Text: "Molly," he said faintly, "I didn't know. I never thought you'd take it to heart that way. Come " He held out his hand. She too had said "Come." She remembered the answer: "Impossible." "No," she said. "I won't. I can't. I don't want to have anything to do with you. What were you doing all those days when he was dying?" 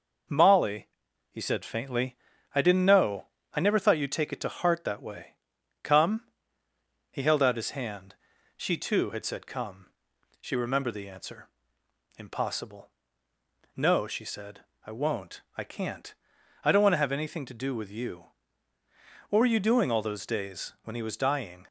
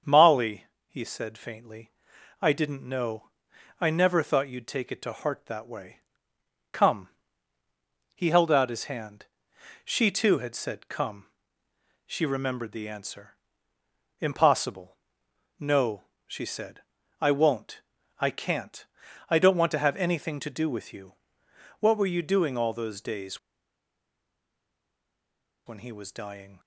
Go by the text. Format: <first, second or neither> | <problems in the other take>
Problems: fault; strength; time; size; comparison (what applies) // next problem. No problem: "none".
first | starts louder than the rest; until 1.2 s; 7 dB // pauses between "days" and "when"; strong; at 23.3 s; 2.2 s long